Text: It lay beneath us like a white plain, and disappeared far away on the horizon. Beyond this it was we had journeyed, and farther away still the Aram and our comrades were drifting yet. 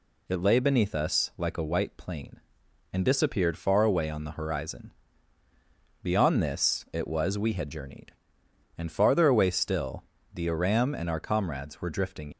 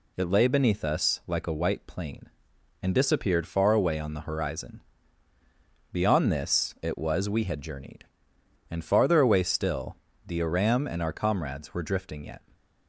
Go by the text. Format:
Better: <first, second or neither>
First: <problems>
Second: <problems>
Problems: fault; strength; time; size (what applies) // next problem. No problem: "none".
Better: second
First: pauses between "still" and "the"; slight; at 10.0 s; 0.30 s long // stops before "yet"; at 12.3 s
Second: pauses between "still" and "the"; slight; at 9.9 s; 0.30 s long